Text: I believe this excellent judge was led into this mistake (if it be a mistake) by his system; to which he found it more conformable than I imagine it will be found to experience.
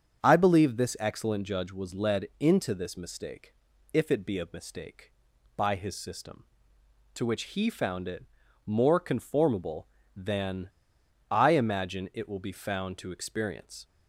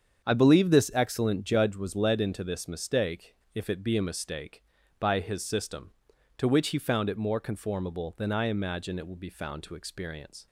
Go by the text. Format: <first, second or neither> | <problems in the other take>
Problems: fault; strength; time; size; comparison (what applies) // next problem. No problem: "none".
second | starts louder than the rest; strong; until 1.2 s; 7.5 dB; strong in the second // pauses between "it" and "more"; at 8.2 s; 0.42 s long // pauses between "than" and "I"; noticeable; at 10.7 s; 0.60 s long